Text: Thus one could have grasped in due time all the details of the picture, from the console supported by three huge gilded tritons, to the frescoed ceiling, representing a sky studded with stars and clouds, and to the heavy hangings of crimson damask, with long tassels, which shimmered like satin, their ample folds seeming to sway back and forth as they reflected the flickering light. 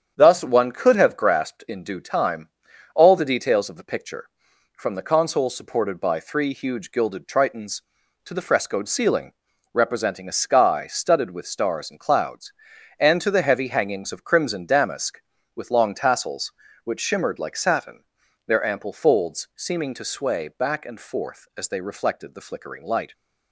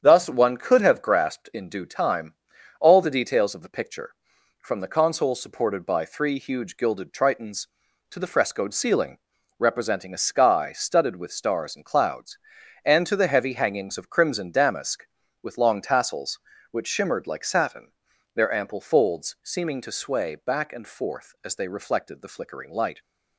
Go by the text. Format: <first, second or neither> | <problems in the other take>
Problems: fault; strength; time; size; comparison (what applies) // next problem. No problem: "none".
neither | starts louder than the rest; strong; the same in both // pauses between "time" and "all"; noticeable; the same in both